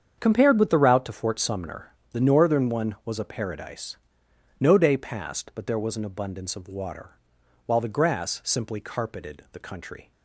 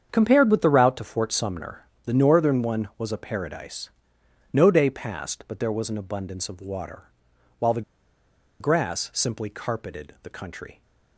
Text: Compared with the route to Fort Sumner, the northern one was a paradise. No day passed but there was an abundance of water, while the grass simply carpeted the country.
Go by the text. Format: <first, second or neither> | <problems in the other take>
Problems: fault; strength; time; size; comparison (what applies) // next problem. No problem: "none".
first | starts louder than the rest; strong; until 1.1 s; 7.5 dB; strong in the first // pauses between "the" and "grass"; noticeable; at 7.8 s; 0.78 s long